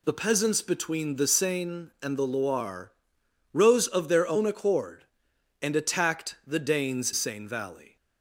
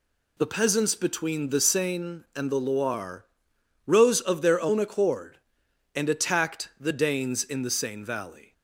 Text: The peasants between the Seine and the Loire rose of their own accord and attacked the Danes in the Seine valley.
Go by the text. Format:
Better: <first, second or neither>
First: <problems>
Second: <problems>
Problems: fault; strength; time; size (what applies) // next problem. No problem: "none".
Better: second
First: pauses between "Loire" and "rose"; noticeable; at 2.9 s; 0.64 s long // skips "in the"; at 7.1 s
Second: pauses between "Loire" and "rose"; noticeable; at 3.2 s; 0.64 s long